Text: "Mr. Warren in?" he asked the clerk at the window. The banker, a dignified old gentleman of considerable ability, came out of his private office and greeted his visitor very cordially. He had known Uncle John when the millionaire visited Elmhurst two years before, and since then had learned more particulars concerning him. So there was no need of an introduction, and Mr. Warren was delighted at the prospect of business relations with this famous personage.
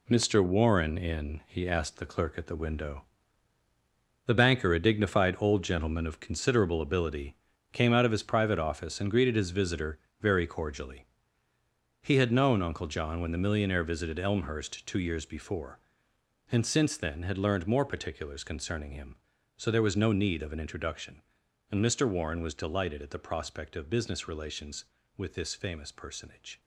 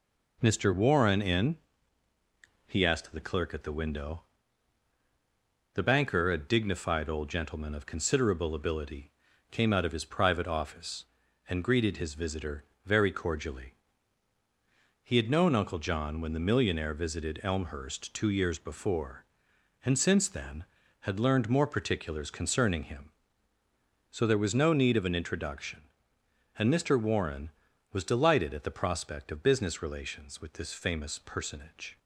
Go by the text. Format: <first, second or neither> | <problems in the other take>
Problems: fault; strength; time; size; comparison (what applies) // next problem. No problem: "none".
second | gets quieter; strong; throughout; 7.5 dB // pauses between "visitor" and "very"; slight; at 9.9 s; 0.22 s long; slight in the second